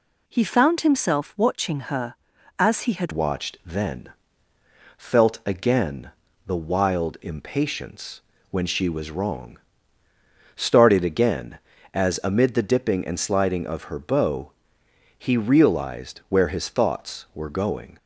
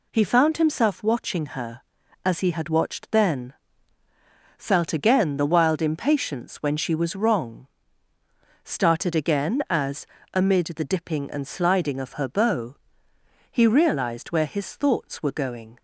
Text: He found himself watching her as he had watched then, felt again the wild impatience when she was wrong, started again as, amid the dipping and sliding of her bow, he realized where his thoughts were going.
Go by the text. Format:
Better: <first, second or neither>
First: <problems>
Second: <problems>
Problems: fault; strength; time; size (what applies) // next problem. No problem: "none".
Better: second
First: changes voice at "watched"; from 3.1 s on; 14.8 s long // pauses between "again" and "the"; slight; at 6.1 s; 0.34 s long // pauses between "impatience" and "when"; slight; at 8.2 s; 0.28 s long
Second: none